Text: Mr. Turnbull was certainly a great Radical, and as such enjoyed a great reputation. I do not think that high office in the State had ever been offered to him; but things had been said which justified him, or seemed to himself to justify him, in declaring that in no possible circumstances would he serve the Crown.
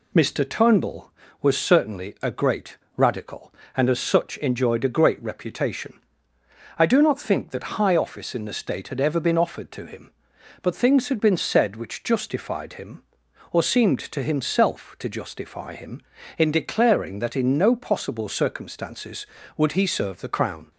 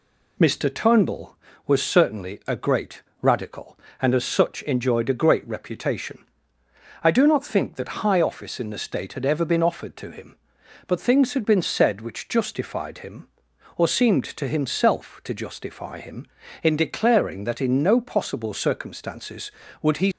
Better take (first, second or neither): first